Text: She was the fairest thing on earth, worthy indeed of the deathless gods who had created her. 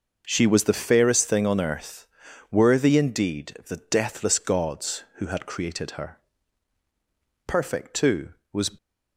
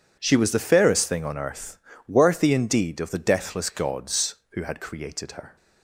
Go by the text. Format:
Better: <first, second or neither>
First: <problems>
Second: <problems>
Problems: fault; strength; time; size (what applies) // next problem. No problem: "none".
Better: second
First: goes on to say "Perfect too was"; noticeable; from 7.4 s on; 1.2 s long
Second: none